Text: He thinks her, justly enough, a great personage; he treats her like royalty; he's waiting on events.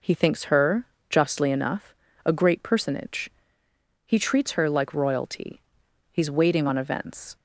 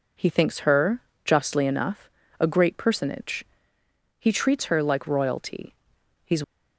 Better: first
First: none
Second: stops before "waiting on events"; at 6.4 s

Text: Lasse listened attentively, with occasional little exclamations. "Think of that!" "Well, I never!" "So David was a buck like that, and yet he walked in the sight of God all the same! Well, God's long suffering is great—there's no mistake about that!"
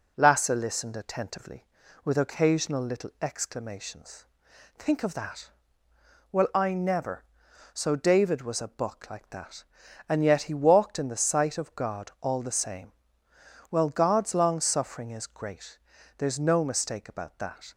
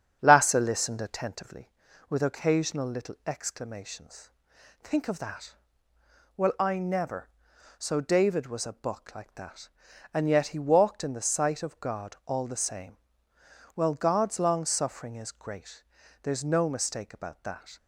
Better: first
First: none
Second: starts louder than the rest; strong; until 1.3 s; 8 dB

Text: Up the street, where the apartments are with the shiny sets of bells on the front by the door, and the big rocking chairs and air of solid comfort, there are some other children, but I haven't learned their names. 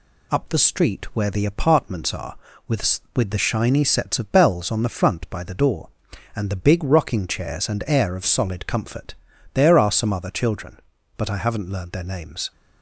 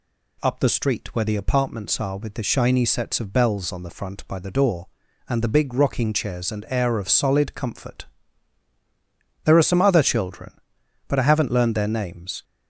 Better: second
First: says "with" twice; at 3.1 s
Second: none

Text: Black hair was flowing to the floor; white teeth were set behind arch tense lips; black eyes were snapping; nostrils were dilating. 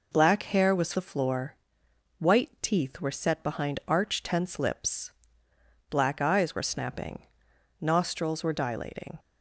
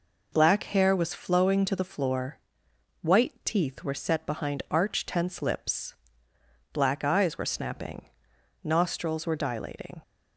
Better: second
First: skips "flowing to"; at 0.9 s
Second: none

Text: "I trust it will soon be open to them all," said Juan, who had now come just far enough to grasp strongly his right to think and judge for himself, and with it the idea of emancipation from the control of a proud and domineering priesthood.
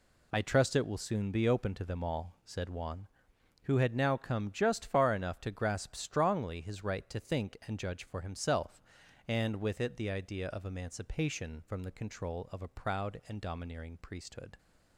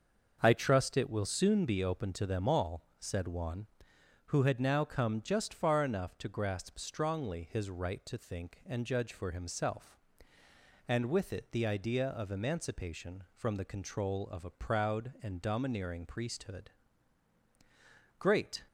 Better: first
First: none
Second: starts louder than the rest; until 1.4 s; 6.5 dB // goes on to say "Great"; slight; from 18.1 s on; 0.42 s long

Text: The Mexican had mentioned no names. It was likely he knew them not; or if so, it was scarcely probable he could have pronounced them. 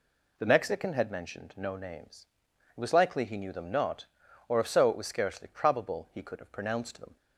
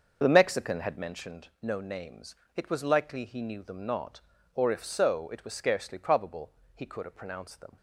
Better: first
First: none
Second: starts louder than the rest; until 1.2 s; 6.5 dB // pauses between "probable" and "he"; slight; at 6.5 s; 0.24 s long

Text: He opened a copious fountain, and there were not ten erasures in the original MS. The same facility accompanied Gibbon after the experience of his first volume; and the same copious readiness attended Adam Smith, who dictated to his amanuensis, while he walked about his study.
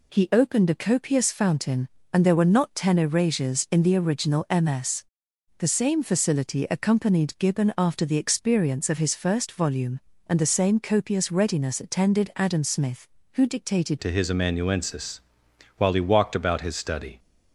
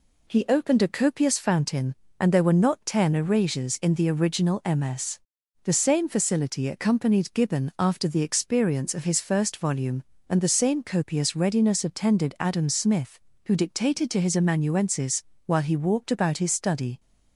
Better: second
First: changes voice at "to"; from 13.9 s on; 3.2 s long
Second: none

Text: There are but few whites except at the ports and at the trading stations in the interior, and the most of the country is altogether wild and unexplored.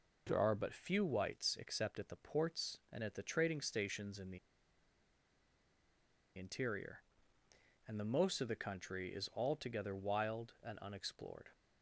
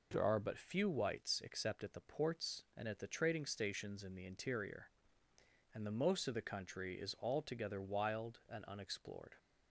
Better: second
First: pauses between "the" and "interior"; strong; at 4.3 s; 1.9 s long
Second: none

